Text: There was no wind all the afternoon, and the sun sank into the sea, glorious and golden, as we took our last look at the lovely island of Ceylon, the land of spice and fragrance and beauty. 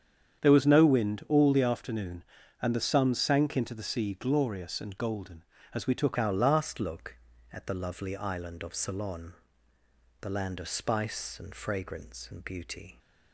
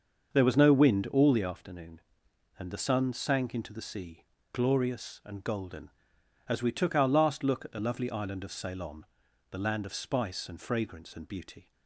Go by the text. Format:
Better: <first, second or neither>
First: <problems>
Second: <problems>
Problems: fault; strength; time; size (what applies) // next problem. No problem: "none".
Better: second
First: starts louder than the rest; strong; until 1.4 s; 8 dB // changes voice at "our"; from 6.1 s on; 6.8 s long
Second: starts louder than the rest; until 1.3 s; 6.5 dB